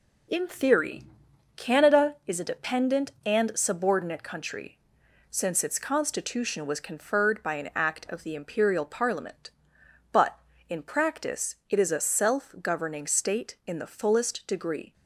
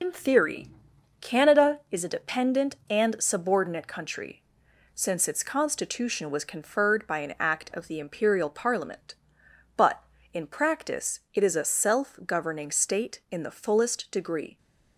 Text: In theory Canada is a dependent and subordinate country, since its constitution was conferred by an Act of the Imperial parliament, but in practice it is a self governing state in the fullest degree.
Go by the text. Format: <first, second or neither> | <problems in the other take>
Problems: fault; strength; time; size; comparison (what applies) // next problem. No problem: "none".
first | loses the start of "In"; at 0.0 s; 80 ms // pauses between "theory" and "Canada"; noticeable; at 0.6 s; 0.56 s long; noticeable in the first // pauses between "practice" and "it"; slight; at 11.1 s; 0.16 s long; slight in the first